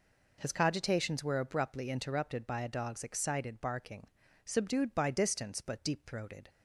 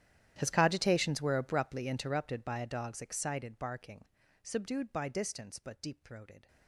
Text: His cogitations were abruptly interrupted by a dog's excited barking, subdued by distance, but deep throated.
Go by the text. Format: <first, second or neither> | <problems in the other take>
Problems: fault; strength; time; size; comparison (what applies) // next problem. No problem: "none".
first | gets quieter; strong; throughout; 22 dB